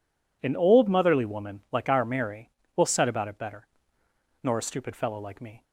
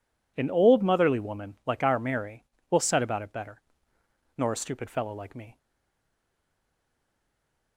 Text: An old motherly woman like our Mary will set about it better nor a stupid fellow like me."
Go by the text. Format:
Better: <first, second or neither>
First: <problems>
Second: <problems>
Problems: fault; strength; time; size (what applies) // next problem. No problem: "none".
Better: first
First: pauses between "better" and "nor"; noticeable; at 3.6 s; 0.74 s long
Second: pauses between "better" and "nor"; noticeable; at 3.6 s; 0.74 s long // stays silent after the last word; from 5.5 s on; 2.2 s long